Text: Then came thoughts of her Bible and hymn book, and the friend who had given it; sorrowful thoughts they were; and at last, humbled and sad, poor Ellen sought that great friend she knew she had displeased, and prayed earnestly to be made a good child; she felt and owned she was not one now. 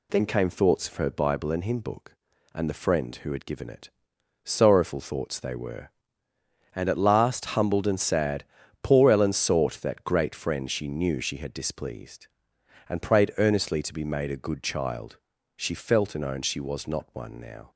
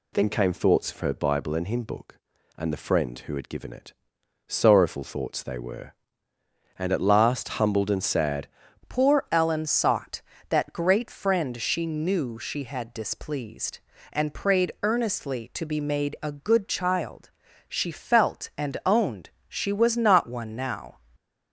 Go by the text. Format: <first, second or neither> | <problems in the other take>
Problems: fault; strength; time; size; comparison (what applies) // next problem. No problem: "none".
first | changes voice at "poor"; from 8.8 s on; 12.1 s long // pauses between "owned" and "she"; slight; at 19.3 s; 0.18 s long // stays silent after the last word; slight; from 20.9 s on; 0.6 s long